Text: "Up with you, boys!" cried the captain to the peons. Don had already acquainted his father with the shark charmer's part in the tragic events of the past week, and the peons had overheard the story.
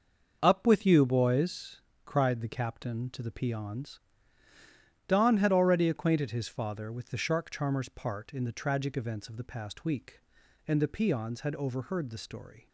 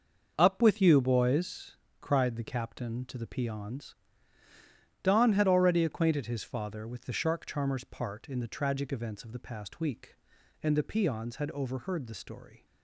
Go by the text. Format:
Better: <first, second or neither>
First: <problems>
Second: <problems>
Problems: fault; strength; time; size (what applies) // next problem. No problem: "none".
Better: neither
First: starts louder than the rest; until 1.4 s; 6 dB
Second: starts louder than the rest; until 1.3 s; 6 dB